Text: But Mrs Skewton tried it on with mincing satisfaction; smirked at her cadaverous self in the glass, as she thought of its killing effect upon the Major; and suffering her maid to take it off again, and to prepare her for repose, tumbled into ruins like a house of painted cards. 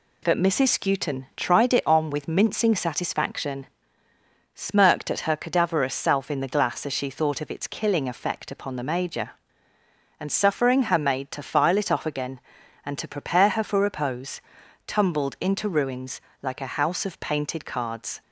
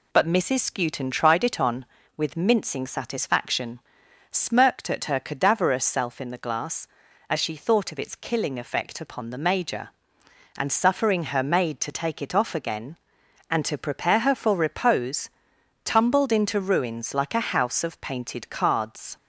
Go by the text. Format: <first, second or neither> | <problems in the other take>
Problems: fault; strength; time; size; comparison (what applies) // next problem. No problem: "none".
second | says "file" for "take"; at 11.4 s // pauses between "ruins" and "like"; slight; at 16.2 s; 0.20 s long